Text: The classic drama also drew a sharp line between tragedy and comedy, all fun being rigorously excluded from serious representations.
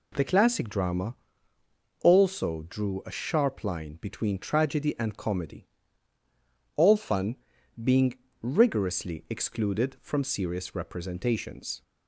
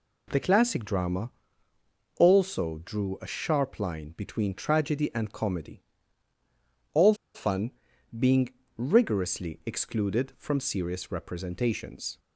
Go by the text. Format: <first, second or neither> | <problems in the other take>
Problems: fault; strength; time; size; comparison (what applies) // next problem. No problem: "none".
first | pauses between "drama" and "also"; noticeable; at 1.3 s; 0.88 s long; noticeable in the first // pauses between "all" and "fun"; slight; at 7.1 s; 0.19 s long // pauses between "fun" and "being"; noticeable; at 7.7 s; 0.46 s long; noticeable in the first // pauses between "being" and "rigorously"; slight; at 8.4 s; 0.28 s long; slight in the first